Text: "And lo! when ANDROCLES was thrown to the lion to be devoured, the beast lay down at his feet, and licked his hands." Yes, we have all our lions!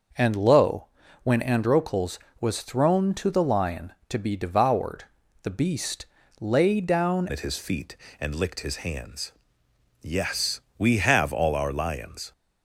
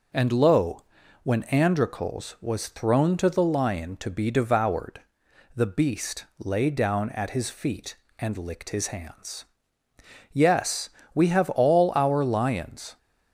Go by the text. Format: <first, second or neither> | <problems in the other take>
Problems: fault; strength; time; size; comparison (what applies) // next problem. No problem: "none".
second | pauses between "beast" and "lay"; slight; at 6.0 s; 0.36 s long // changes voice at "at"; from 7.2 s on; 5.1 s long